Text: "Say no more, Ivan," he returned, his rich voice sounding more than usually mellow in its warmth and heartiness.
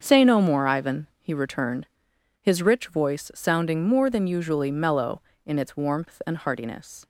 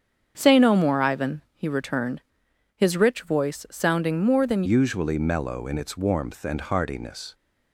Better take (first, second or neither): first